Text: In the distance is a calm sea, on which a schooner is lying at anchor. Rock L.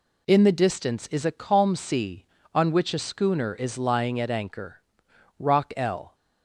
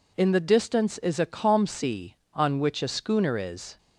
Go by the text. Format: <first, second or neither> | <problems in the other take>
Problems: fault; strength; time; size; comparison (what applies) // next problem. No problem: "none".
first | stops before "lying at anchor Rock L"; at 3.7 s